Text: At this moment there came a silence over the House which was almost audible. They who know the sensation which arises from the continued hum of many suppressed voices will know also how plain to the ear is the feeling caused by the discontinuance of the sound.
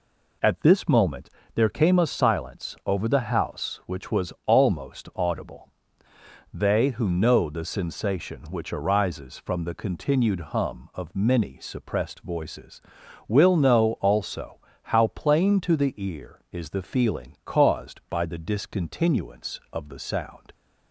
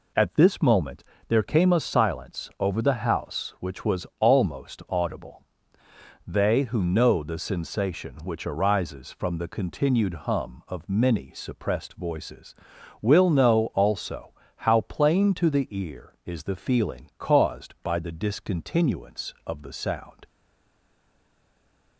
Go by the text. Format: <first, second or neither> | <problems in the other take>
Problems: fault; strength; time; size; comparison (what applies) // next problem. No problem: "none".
first | pauses between "moment" and "there"; slight; at 1.0 s; 0.26 s long; slight in the first // pauses between "also" and "how"; slight; at 14.3 s; 0.24 s long; slight in the first // stays silent after the last word; noticeable; from 20.2 s on; 1.7 s long